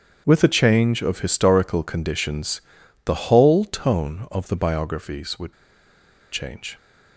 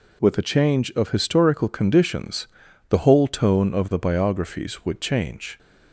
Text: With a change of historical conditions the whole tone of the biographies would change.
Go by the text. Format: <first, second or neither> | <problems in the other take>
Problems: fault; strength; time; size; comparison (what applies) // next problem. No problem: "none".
second | starts louder than the rest; strong; until 1.2 s; 7.5 dB // pauses between "conditions" and "the"; at 2.6 s; 0.42 s long; also in the second // pauses between "would" and "change"; noticeable; at 5.5 s; 0.80 s long